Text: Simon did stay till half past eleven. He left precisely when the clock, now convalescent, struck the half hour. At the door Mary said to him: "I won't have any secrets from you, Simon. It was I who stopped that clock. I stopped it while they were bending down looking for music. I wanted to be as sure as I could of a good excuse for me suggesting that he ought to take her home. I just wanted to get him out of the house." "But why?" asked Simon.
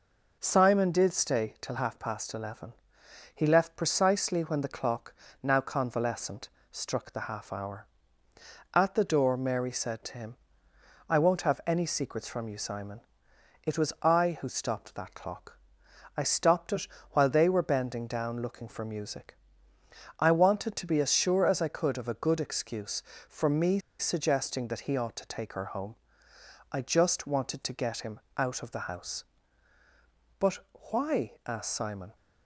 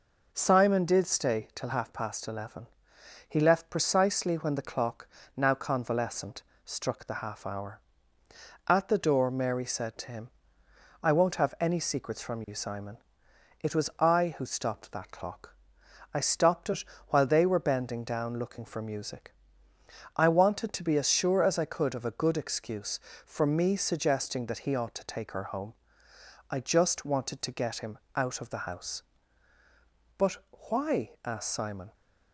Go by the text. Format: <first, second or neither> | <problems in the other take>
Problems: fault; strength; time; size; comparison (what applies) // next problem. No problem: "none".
second | pauses between "it" and "while"; slight; at 16.8 s; 0.26 s long; slight in the second // pauses between "me" and "suggesting"; slight; at 23.7 s; 0.21 s long // pauses between "him" and "out"; slight; at 28.2 s; 0.16 s long; slight in the second // pauses between "But" and "why"; slight; at 30.5 s; 0.32 s long; slight in the second